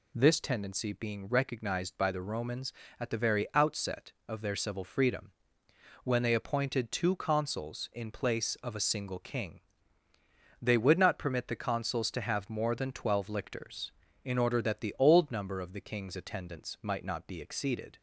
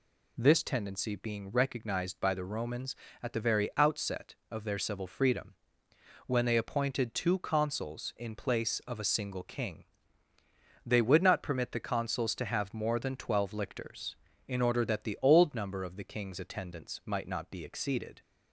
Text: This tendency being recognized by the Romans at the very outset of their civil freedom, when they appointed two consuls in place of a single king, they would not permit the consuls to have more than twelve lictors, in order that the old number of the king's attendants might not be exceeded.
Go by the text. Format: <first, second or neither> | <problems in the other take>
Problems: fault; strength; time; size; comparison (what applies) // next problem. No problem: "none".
neither | none